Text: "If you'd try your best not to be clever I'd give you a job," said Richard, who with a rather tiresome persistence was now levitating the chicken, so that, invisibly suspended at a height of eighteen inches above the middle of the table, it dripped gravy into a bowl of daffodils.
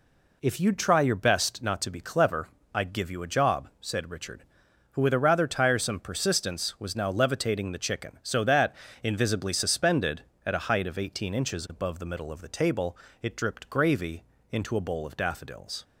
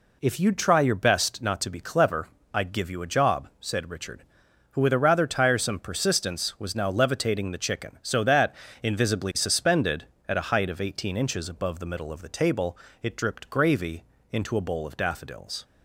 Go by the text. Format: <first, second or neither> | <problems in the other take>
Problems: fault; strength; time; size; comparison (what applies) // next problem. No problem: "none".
neither | pauses between "clever" and "I'd"; slight; the same in both // pauses between "gravy" and "into"; slight; the same in both